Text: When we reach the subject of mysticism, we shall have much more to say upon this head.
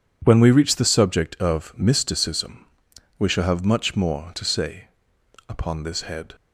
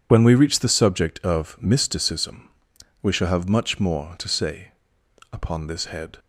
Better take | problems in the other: first | loses the start of "When"; at 0.0 s; 40 ms // pauses between "say" and "upon"; noticeable; at 4.6 s; 0.64 s long; noticeable in the first

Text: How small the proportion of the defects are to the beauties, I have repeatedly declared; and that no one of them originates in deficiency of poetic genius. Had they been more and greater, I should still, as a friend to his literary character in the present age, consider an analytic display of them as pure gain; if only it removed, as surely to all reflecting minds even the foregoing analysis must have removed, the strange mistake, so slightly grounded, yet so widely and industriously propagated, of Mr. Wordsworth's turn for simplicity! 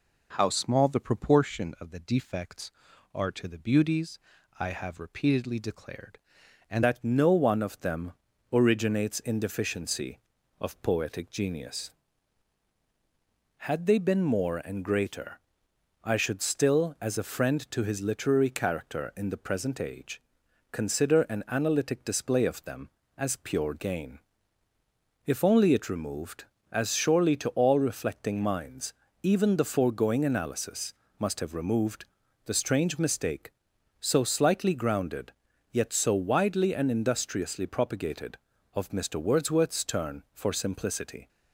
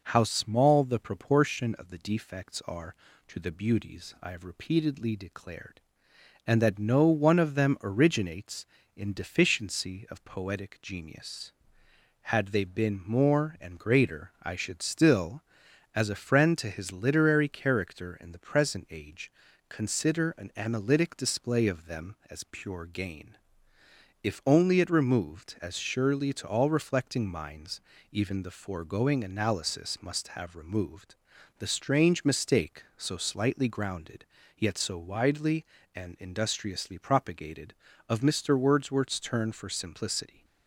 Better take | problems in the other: second | changes voice at "that"; from 6.8 s on; 34.4 s long // pauses between "them" and "originates"; slight; at 8.1 s; 0.36 s long // pauses between "minds" and "even"; slight; at 28.9 s; 0.30 s long; slight in the second // pauses between "analysis" and "must"; slight; at 30.9 s; 0.26 s long

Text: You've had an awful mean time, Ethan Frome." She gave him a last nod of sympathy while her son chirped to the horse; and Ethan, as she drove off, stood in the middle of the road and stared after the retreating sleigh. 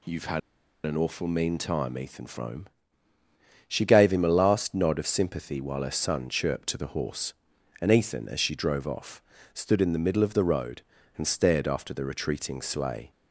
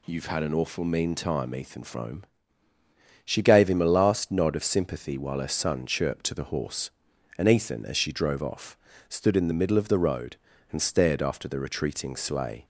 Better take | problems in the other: second | pauses between "had" and "an"; noticeable; at 0.3 s; 0.46 s long

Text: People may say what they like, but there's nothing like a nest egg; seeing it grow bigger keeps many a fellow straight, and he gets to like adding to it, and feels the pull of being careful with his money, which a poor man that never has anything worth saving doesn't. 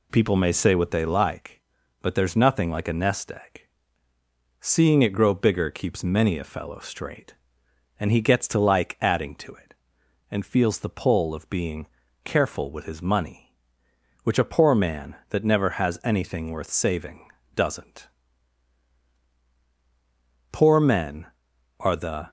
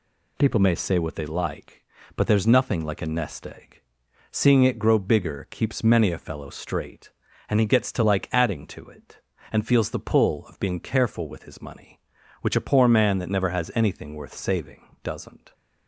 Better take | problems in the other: second | pauses between "being" and "careful"; at 11.8 s; 0.38 s long // pauses between "saving" and "doesn't"; slight; at 17.2 s; 0.26 s long; slight in the second // goes on to say "Poor men are the"; strong; from 20.5 s on; 1.7 s long

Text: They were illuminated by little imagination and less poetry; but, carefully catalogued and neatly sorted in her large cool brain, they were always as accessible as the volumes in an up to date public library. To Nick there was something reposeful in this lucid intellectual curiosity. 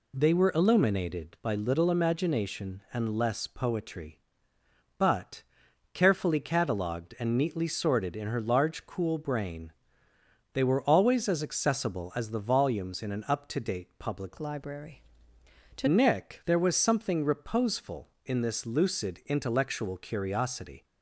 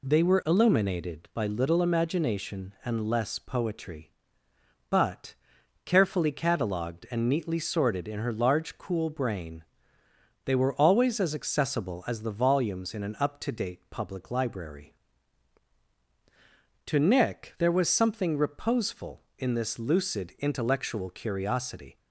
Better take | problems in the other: second | changes voice from "library" to "To"; from 14.3 to 15.8 s; 1.5 s long

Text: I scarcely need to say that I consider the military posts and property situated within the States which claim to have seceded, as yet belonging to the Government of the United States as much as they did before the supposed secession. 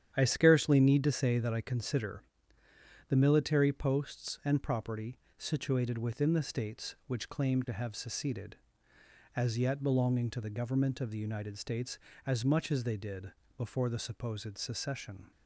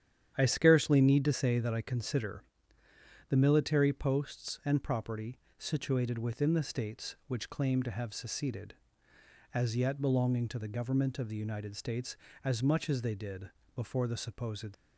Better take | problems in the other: first | starts louder than the rest; strong; until 1.3 s; 10 dB; strong in the first // pauses between "consider" and "the"; noticeable; at 2.4 s; 0.82 s long; noticeable in the first // pauses between "property" and "situated"; slight; at 5.3 s; 0.20 s long; slight in the first // pauses between "did" and "before"; slight; at 13.5 s; 0.24 s long; slight in the first // stops before "secession"; at 14.7 s

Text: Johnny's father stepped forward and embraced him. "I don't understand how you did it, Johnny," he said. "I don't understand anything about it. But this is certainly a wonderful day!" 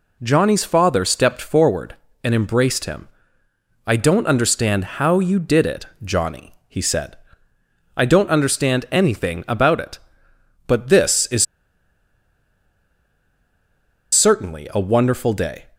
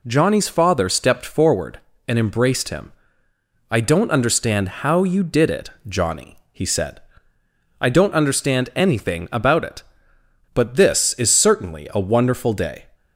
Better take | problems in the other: second | pauses between "is" and "certainly"; strong; at 11.4 s; 2.6 s long

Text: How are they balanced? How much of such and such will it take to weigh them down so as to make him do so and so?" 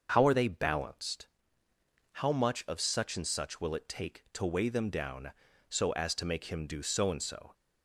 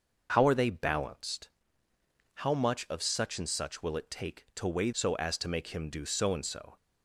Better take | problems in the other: first | starts louder than the rest; noticeable; until 1.3 s; 6 dB; also in the first // skips "them down"; at 4.9 s

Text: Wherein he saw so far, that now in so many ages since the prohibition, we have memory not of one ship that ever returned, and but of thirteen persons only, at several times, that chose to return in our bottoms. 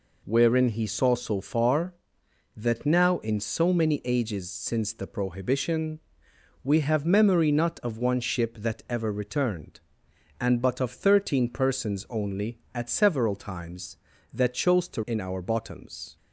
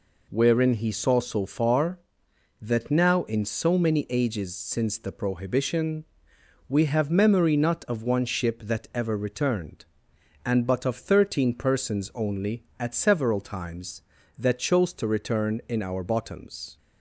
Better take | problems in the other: second | skips "return"; at 15.0 s

